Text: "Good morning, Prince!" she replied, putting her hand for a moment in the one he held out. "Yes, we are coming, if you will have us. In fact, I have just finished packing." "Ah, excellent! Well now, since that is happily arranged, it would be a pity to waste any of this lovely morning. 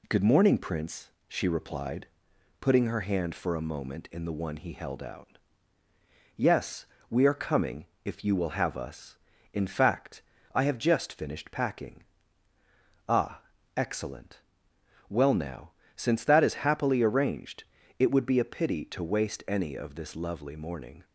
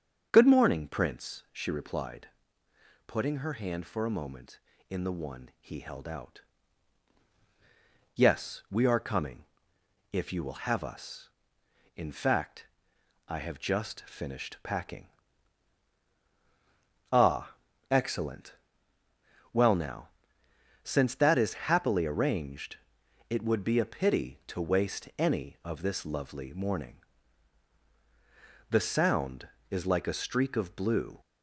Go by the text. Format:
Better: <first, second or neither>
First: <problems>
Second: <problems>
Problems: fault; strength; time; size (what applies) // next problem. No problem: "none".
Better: first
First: none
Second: starts louder than the rest; until 1.3 s; 7 dB // goes on to say "The Sound is like a streak of blue"; strong; from 28.7 s on; 2.5 s long